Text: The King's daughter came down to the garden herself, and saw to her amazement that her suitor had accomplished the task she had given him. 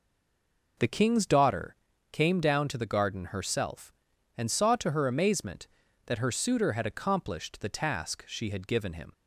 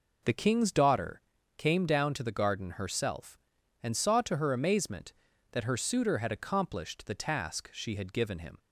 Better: second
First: stays silent before the first word; slight; until 0.7 s; 0.7 s long // pauses between "daughter" and "came"; at 1.7 s; 0.38 s long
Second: pauses between "daughter" and "came"; at 1.1 s; 0.38 s long

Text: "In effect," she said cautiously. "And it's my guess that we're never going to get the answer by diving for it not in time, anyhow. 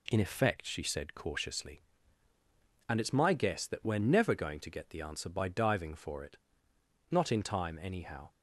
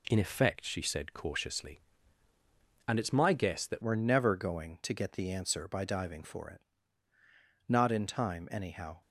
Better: first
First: pauses between "it" and "not"; noticeable; at 6.3 s; 0.74 s long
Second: changes voice at "we're"; from 3.8 s on; 5.2 s long // pauses between "it" and "not"; at 6.6 s; 1.0 s long

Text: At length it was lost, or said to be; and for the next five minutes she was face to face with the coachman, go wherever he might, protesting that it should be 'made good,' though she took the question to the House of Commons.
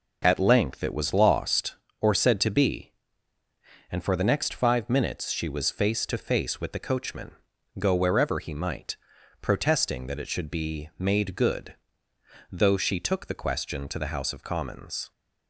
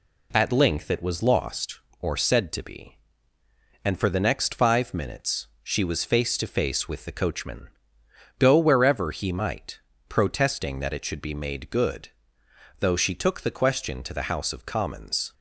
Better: neither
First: none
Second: none

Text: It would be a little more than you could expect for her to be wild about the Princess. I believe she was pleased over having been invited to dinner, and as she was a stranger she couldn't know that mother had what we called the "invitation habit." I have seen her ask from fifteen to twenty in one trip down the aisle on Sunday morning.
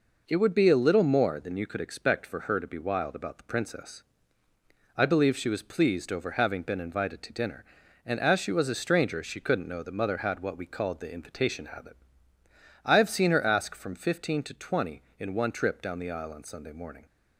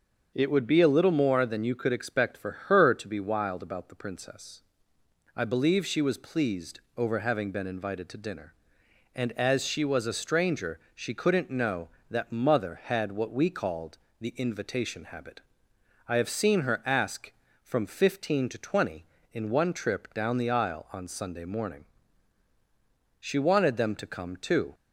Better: first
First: none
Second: starts louder than the rest; until 1.3 s; 6.5 dB // pauses between "for" and "her"; slight; at 2.5 s; 0.16 s long // pauses between "pleased" and "over"; slight; at 6.7 s; 0.18 s long // pauses between "stranger" and "she"; slight; at 10.7 s; 0.16 s long // pauses between "called" and "the"; slight; at 13.9 s; 0.20 s long // goes on to say "She wanted them to come too"; from 23.1 s on; 1.5 s long

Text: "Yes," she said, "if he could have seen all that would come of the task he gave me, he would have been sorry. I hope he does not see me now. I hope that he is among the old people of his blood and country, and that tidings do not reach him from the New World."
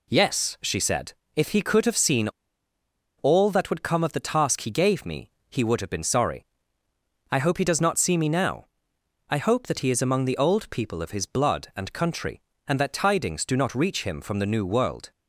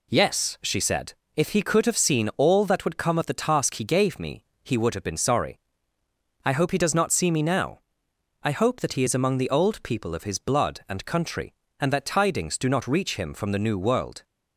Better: second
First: pauses between "seen" and "all"; noticeable; at 2.2 s; 0.88 s long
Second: none

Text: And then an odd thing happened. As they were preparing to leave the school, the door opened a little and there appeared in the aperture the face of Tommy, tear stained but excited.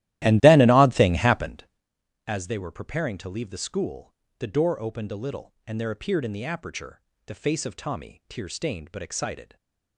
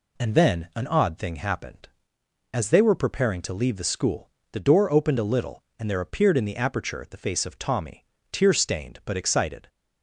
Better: second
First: starts louder than the rest; strong; until 1.7 s; 15 dB // pauses between "aperture" and "the"; slight; at 6.9 s; 0.28 s long // stays silent after the last word; slight; from 9.4 s on; 0.5 s long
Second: none

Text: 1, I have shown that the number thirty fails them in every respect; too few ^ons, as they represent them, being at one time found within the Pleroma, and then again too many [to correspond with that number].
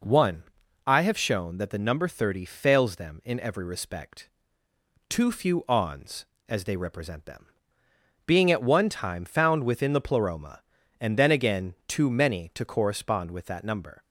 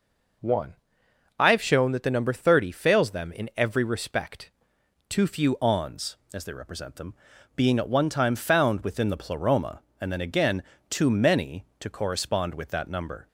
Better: first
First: none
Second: changes voice at "ons"; from 5.6 s on; 7.6 s long // pauses between "again" and "too"; slight; at 10.6 s; 0.28 s long

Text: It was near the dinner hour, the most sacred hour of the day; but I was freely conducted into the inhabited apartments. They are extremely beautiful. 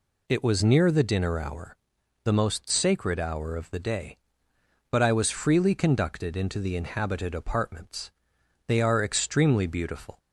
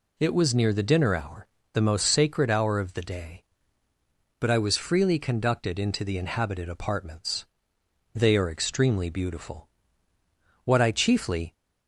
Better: first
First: none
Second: goes on to say "What I chiefly"; noticeable; from 10.6 s on; 0.88 s long

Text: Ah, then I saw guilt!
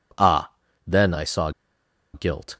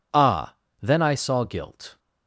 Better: second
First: pauses between "saw" and "guilt"; noticeable; at 1.5 s; 0.63 s long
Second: none

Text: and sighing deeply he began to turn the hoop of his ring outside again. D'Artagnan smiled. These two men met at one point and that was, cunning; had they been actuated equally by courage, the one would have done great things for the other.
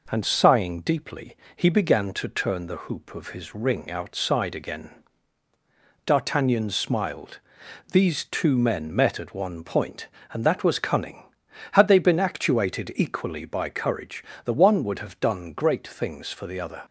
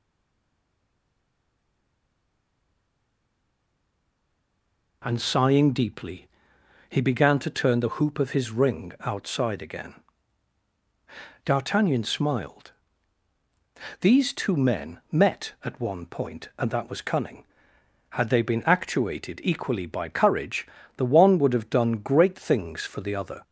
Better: first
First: pauses between "deeply" and "he"; slight; at 1.3 s; 0.20 s long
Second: stays silent before the first word; strong; until 5.0 s; 5.0 s long // pauses between "deeply" and "he"; noticeable; at 6.2 s; 0.62 s long

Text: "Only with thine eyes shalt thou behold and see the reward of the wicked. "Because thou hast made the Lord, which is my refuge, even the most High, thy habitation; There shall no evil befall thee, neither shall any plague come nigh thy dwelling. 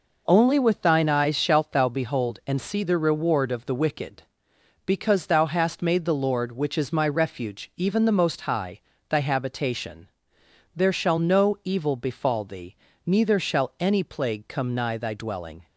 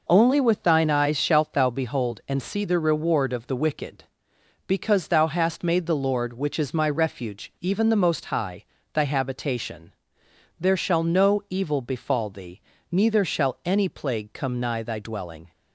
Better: neither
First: none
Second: none

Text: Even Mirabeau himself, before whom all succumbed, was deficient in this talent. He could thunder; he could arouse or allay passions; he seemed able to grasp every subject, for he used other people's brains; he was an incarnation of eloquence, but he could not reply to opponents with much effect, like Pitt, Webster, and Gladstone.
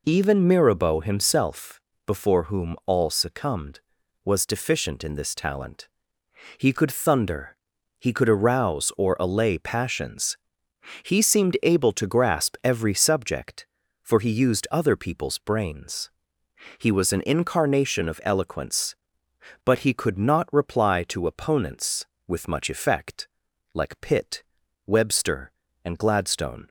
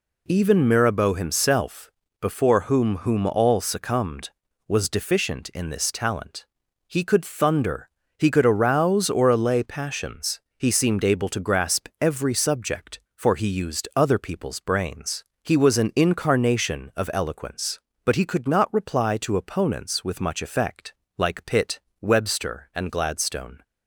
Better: first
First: none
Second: says "whom" twice; at 2.9 s

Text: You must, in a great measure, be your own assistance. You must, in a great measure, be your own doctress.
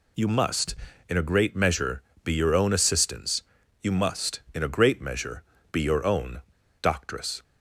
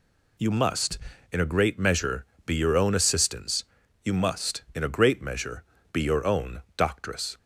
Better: second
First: pauses between "own" and "doctress"; at 6.4 s; 0.39 s long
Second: none

